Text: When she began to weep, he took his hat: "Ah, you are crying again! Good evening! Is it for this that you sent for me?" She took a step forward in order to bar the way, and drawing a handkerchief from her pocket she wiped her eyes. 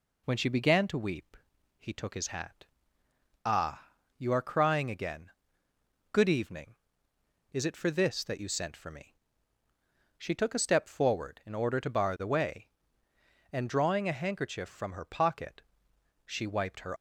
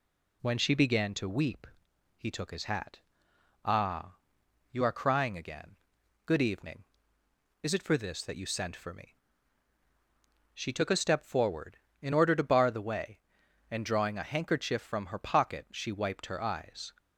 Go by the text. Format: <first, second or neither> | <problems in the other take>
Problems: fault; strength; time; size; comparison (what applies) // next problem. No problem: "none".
second | pauses between "pocket" and "she"; noticeable; at 15.6 s; 0.62 s long // stops before "eyes"; at 16.9 s